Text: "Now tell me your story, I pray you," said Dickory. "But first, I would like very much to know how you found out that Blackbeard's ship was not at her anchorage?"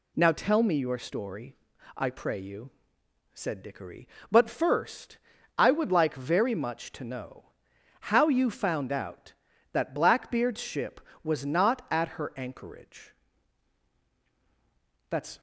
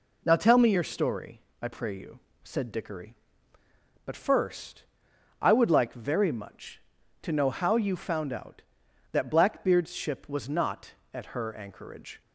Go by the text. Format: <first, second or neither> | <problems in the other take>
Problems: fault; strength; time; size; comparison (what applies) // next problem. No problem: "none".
second | pauses between "know" and "how"; noticeable; at 7.4 s; 0.62 s long // goes on to say "That's"; slight; from 15.0 s on; 0.30 s long